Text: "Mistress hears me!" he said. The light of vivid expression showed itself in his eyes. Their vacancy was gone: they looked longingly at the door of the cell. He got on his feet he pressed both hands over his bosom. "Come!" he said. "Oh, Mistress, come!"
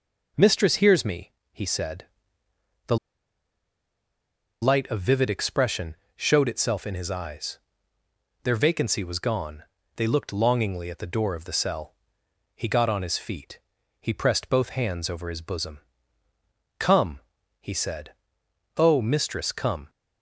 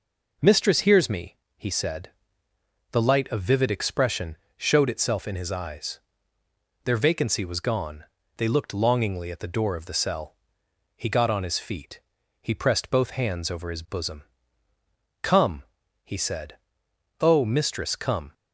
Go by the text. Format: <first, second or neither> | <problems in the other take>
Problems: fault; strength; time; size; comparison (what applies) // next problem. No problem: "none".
second | pauses between "The" and "light"; strong; at 2.9 s; 1.6 s long // pauses between "expression" and "showed"; slight; at 5.9 s; 0.20 s long; slight in the second // pauses between "feet" and "he"; at 13.5 s; 0.40 s long; also in the second